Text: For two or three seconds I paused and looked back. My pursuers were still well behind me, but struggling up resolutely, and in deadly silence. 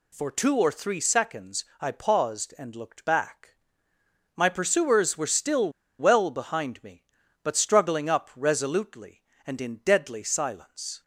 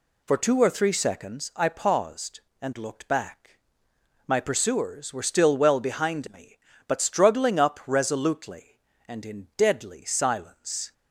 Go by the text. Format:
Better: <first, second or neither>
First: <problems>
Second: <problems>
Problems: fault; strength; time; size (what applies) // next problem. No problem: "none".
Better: second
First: pauses between "seconds" and "I"; slight; at 1.6 s; 0.16 s long // pauses between "still" and "well"; slight; at 5.7 s; 0.27 s long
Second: none